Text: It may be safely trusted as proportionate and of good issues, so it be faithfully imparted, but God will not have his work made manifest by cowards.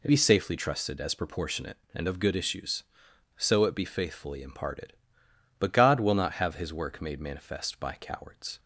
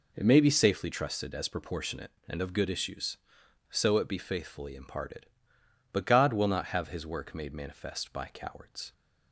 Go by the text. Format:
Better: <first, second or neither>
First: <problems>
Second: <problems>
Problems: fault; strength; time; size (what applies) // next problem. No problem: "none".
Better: second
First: skips "may"; at 0.0 s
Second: none